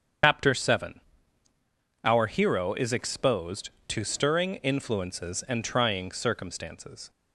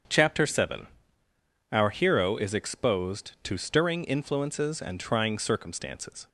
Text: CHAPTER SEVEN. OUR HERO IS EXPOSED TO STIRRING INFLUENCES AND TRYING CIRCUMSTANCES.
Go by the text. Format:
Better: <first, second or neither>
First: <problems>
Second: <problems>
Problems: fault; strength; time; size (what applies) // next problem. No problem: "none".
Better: second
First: loses the start of "CHAPTER"; at 0.2 s; 135 ms // starts louder than the rest; strong; until 2.2 s; 8 dB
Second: starts louder than the rest; strong; until 1.9 s; 7.5 dB